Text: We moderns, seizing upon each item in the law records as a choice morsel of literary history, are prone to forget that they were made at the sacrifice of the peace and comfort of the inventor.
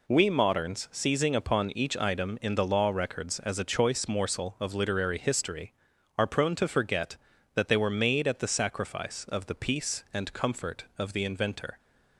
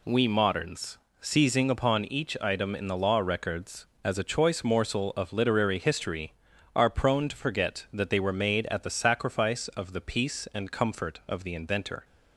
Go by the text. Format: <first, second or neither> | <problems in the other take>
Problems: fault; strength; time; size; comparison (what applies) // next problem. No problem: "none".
neither | none